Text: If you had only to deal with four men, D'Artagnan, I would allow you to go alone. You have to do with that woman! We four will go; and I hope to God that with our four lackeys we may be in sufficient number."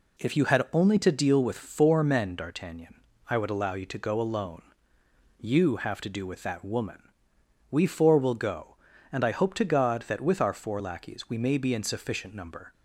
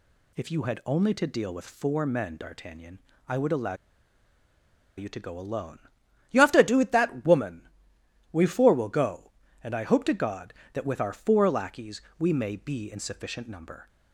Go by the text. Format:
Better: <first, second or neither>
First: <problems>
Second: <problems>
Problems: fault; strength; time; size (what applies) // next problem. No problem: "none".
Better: first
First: none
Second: pauses between "allow" and "you"; at 3.7 s; 1.2 s long // pauses between "lackeys" and "we"; slight; at 12.0 s; 0.16 s long